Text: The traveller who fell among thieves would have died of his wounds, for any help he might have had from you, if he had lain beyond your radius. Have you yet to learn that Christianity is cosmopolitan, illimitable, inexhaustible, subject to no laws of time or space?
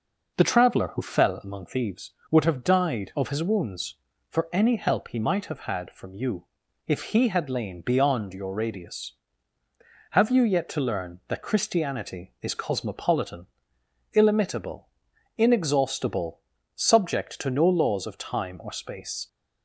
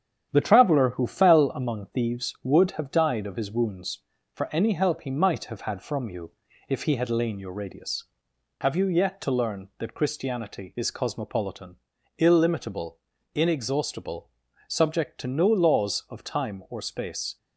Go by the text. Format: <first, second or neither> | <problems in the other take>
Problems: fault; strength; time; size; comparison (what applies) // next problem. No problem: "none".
first | starts louder than the rest; strong; until 1.3 s; 9 dB // skips "beyond"; at 7.3 s